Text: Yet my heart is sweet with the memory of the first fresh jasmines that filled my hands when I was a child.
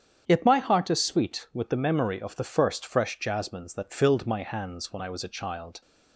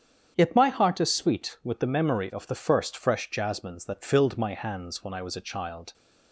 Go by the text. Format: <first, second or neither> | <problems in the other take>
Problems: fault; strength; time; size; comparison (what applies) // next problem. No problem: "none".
neither | starts louder than the rest; strong; the same in both